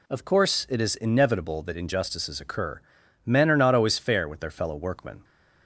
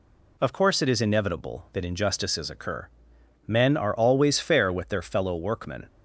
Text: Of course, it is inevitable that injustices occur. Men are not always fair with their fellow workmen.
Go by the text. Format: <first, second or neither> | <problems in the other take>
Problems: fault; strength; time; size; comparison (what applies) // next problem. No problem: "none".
first | skips "not"; at 3.9 s